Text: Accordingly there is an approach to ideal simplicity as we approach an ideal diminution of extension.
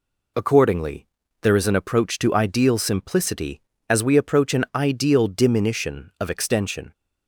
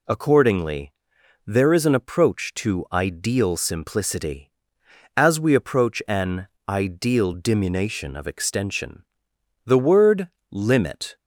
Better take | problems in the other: first | pauses between "Accordingly" and "there"; noticeable; at 0.9 s; 0.54 s long; slight in the first // pauses between "an" and "ideal"; slight; at 6.4 s; 0.21 s long // goes on to say "The word limit"; from 9.6 s on; 1.5 s long

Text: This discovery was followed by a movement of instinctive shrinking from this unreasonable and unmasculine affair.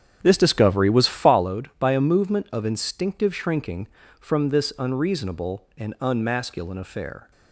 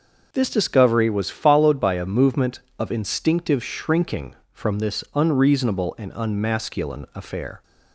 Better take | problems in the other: second | starts louder than the rest; strong; until 1.4 s; 8 dB

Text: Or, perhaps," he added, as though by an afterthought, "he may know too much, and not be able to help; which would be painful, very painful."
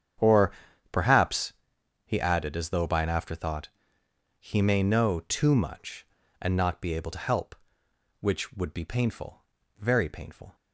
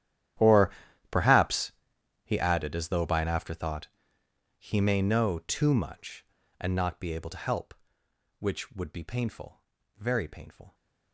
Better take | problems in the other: first | gets quieter; strong; throughout; 20 dB // starts louder than the rest; strong; until 2.3 s; 11 dB; strong in the first

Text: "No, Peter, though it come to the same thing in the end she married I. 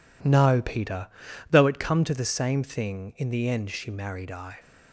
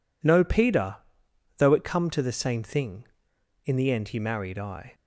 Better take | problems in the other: first | says "he" for "she"; at 4.0 s

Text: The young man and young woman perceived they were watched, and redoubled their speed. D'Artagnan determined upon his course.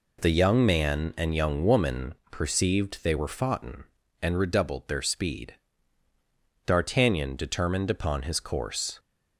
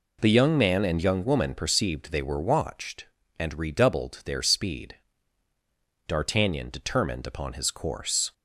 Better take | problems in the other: second | pauses between "woman" and "perceived"; slight; at 2.1 s; 0.16 s long // says "foughten" for "watched"; at 3.2 s

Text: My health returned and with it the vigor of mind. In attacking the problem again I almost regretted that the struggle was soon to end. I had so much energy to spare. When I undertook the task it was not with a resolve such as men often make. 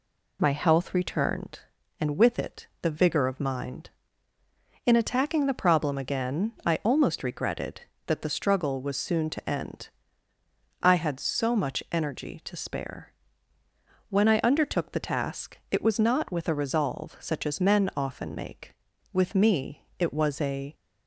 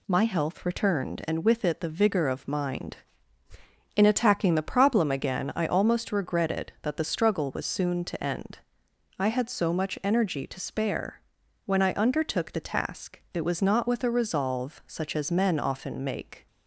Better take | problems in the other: second | goes on to say "With me it was a"; from 19.1 s on; 1.6 s long

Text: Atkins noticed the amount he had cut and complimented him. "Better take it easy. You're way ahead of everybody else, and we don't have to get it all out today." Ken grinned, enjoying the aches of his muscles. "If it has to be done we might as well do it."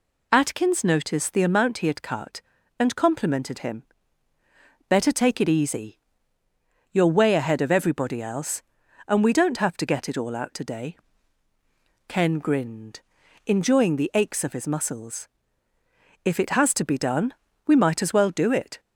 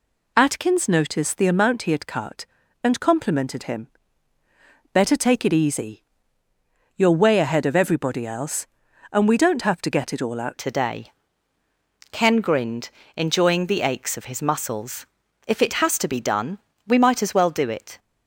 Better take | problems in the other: first | changes voice at "today"; from 10.5 s on; 7.4 s long // pauses between "done" and "we"; slight; at 16.5 s; 0.28 s long; slight in the first

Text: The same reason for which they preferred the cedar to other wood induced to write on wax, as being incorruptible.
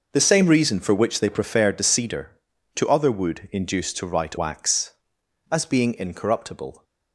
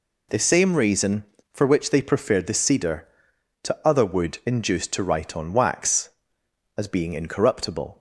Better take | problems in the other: second | skips "on"; at 4.3 s

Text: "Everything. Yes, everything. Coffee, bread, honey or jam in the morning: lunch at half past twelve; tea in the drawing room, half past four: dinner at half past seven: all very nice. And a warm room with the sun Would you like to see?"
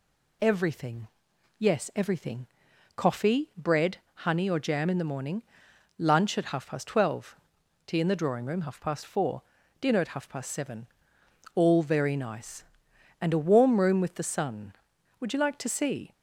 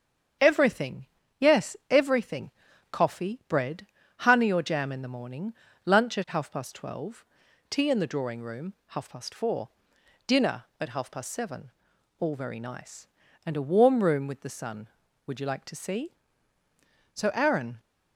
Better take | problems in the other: first | starts louder than the rest; strong; until 1.7 s; 7.5 dB // goes on to say "So Aaron"; noticeable; from 17.1 s on; 0.66 s long

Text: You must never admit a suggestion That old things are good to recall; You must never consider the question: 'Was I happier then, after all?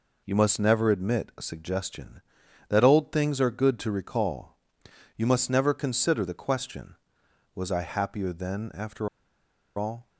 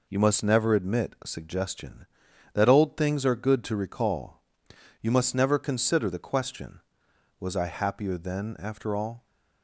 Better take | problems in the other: second | pauses between "after" and "all"; noticeable; at 9.0 s; 0.70 s long

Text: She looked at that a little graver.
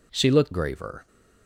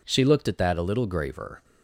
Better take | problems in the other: second | skips "at that a little"; at 0.5 s

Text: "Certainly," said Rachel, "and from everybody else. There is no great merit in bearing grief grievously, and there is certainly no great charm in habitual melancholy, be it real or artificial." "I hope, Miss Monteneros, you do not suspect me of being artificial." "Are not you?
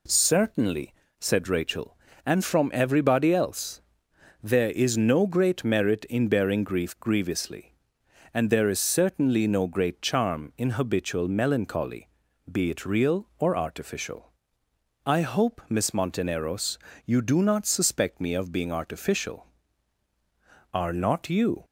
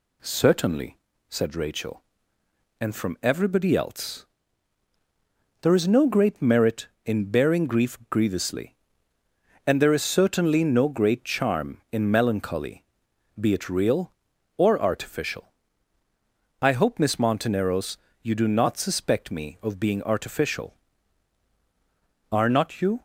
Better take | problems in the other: first | skips "habitual"; at 12.1 s

